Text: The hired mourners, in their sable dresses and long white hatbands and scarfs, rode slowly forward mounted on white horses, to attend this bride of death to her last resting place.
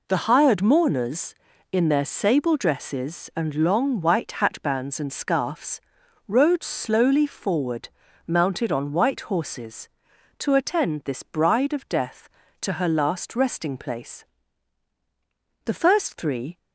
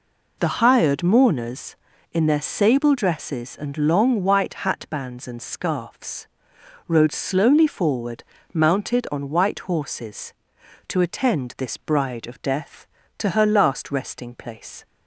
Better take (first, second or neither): second